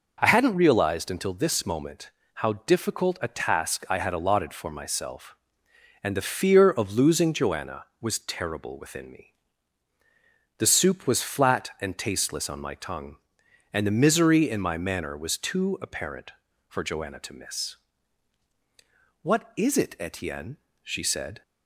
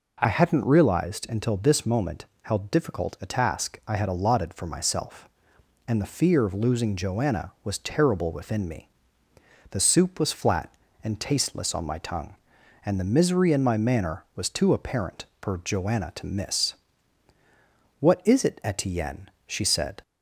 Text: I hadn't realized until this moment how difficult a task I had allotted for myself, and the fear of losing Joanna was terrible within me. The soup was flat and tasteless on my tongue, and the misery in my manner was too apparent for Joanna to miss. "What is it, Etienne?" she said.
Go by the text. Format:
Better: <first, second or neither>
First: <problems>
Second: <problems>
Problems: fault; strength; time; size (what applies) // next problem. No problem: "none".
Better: first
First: pauses between "moment" and "how"; slight; at 2.0 s; 0.24 s long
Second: changes voice at "hadn't"; from 0.2 s on; 19.8 s long // pauses between "moment" and "how"; slight; at 2.2 s; 0.16 s long